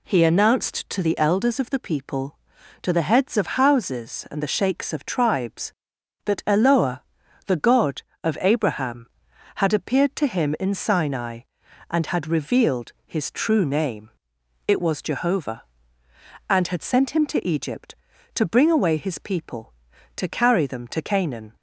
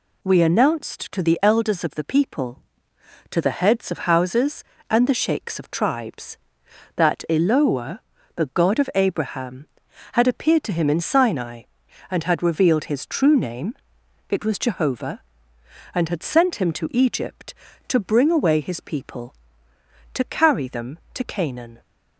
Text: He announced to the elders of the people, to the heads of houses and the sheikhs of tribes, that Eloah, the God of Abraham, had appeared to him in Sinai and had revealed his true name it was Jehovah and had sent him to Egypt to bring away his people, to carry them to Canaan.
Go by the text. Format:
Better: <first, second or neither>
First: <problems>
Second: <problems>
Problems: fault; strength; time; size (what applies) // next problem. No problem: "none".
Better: first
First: pauses between "name" and "it"; noticeable; at 14.1 s; 0.56 s long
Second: says "We" for "He"; at 0.2 s // pauses between "name" and "it"; noticeable; at 13.7 s; 0.56 s long